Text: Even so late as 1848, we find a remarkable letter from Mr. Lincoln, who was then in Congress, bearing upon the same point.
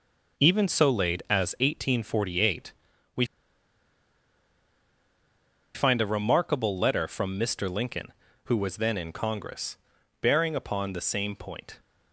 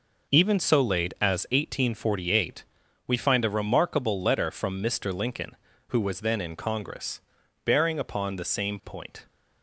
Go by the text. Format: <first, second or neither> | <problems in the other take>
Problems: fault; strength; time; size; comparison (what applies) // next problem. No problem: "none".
second | pauses between "we" and "find"; strong; at 3.2 s; 2.5 s long